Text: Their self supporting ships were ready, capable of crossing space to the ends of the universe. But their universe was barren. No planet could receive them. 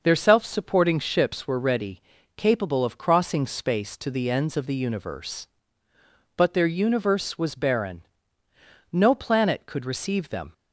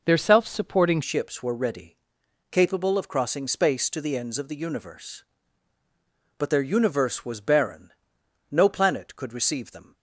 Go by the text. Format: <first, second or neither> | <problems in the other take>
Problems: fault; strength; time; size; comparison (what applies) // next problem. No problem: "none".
first | changes voice at "ships"; from 1.0 s on; 8.9 s long